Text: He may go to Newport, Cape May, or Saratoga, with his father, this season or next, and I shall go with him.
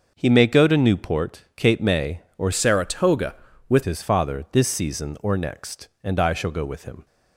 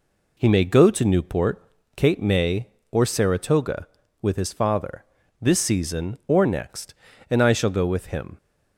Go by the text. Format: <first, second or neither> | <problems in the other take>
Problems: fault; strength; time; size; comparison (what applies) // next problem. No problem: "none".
second | starts louder than the rest; until 1.1 s; 6 dB // changes voice from "Saratoga" to "with"; from 2.5 to 3.8 s; 1.3 s long